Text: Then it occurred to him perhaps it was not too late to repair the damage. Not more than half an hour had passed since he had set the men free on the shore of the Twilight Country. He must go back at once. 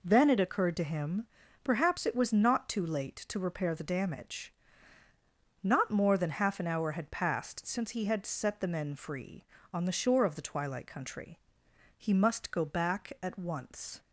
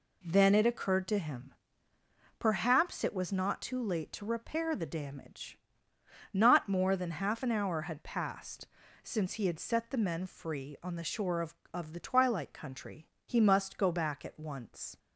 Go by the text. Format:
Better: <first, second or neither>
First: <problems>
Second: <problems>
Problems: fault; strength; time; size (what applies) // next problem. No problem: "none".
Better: first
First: pauses between "him" and "perhaps"; slight; at 1.2 s; 0.36 s long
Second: pauses between "him" and "perhaps"; noticeable; at 1.5 s; 0.84 s long // pauses between "passed" and "since"; slight; at 8.6 s; 0.35 s long // says "of" twice; at 11.7 s